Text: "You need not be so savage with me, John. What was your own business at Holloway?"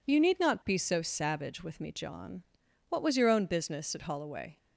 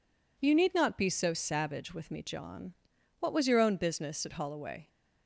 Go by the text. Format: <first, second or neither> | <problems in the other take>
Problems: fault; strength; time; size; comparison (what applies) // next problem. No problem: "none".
neither | none